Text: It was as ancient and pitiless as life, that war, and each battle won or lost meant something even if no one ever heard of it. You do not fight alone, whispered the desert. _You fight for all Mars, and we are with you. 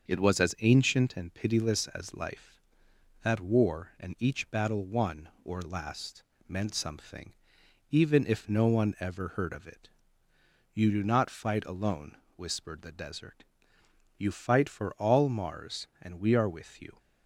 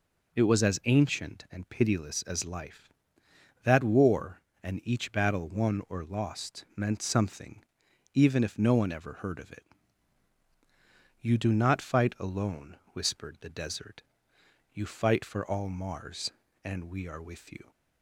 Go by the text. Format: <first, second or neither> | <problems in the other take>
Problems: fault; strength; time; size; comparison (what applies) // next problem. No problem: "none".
second | starts louder than the rest; until 1.1 s; 6 dB // says "last" for "lost"; at 5.6 s // pauses between "something" and "even"; noticeable; at 7.3 s; 0.60 s long; noticeable in the second